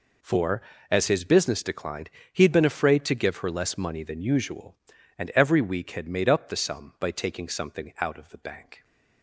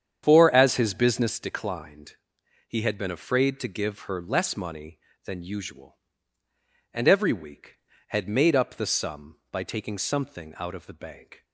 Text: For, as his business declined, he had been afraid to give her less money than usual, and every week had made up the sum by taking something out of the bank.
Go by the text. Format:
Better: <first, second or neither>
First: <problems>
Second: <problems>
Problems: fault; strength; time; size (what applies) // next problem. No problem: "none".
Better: first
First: none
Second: starts louder than the rest; strong; until 1.5 s; 8 dB